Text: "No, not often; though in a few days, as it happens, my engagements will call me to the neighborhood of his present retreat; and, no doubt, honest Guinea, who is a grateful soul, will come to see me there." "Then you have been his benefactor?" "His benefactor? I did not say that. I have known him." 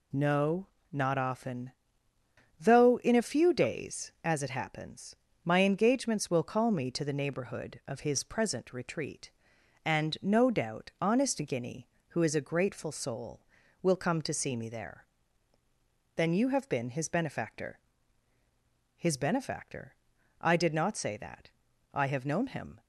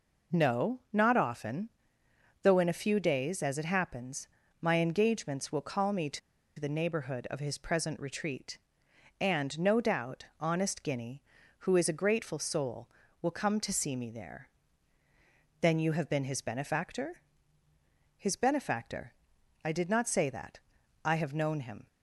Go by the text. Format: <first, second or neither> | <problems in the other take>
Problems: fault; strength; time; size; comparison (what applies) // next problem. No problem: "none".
first | pauses between "to" and "the"; at 6.1 s; 0.39 s long